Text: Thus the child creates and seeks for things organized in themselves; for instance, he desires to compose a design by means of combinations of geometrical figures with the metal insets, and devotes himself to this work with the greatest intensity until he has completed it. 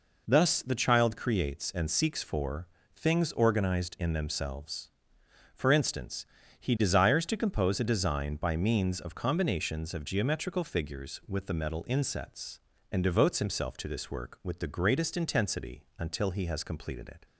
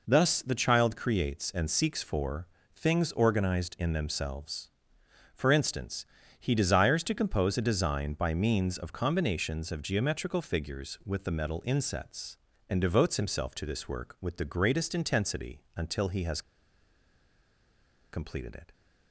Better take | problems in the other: first | pauses between "for" and "things"; slight; at 2.4 s; 0.28 s long; slight in the first // pauses between "has" and "completed"; strong; at 16.4 s; 1.7 s long

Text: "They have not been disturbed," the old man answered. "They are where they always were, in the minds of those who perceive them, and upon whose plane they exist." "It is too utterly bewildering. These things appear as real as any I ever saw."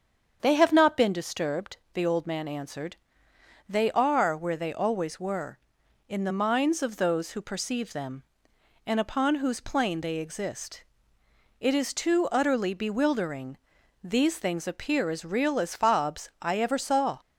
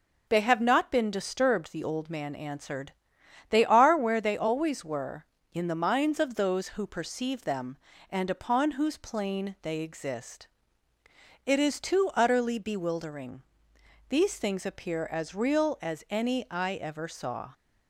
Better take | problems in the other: second | starts louder than the rest; strong; until 1.4 s; 7.5 dB // says "fobs" for "any"; at 15.7 s

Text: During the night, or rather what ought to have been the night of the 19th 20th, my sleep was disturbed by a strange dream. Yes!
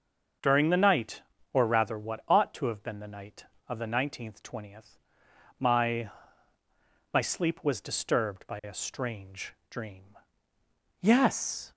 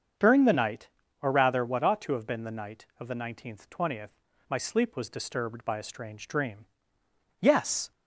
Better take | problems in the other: second | starts louder than the rest; until 1.7 s; 6 dB; also in the second // says "my" twice; at 7.1 s // pauses between "strange" and "dream"; slight; at 9.5 s; 0.16 s long

